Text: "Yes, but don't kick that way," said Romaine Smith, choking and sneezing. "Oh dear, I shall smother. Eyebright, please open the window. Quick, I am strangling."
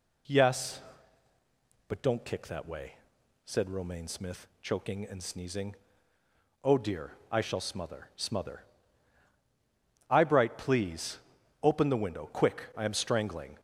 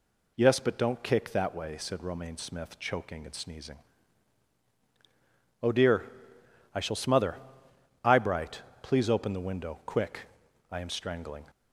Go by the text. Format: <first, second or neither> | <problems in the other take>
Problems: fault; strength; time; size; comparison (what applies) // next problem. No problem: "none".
second | says "smother" twice; at 8.1 s // pauses between "please" and "open"; at 11.1 s; 0.44 s long